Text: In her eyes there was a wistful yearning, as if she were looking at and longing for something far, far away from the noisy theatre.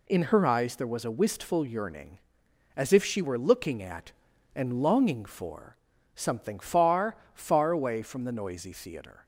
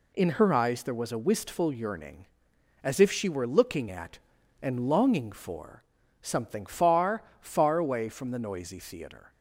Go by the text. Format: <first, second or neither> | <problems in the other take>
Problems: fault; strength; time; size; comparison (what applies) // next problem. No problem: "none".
neither | pauses between "for" and "something"; the same in both